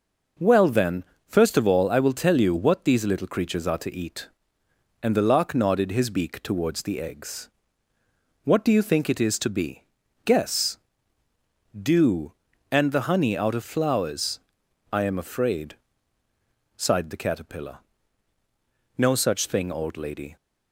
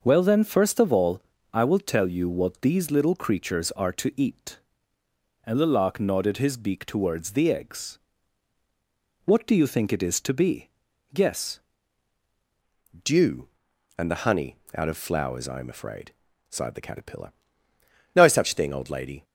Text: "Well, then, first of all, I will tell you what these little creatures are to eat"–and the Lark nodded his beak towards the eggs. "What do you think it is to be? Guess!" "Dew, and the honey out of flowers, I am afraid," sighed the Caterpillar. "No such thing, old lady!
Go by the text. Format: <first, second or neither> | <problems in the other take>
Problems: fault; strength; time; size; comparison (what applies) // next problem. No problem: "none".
first | changes voice at "Dew"; from 13.0 s on; 6.2 s long // pauses between "honey" and "out"; slight; at 14.5 s; 0.18 s long